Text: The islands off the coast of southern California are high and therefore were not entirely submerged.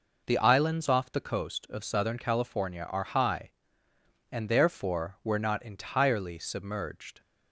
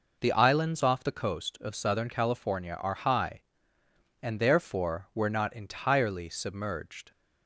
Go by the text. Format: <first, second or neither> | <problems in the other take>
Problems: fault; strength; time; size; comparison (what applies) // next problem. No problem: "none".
neither | none